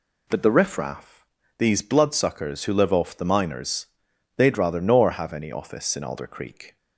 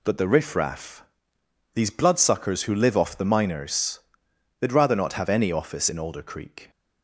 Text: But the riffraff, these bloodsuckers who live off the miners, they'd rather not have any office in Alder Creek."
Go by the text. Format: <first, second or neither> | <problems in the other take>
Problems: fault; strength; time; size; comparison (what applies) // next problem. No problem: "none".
second | says "nor" for "not"; at 4.8 s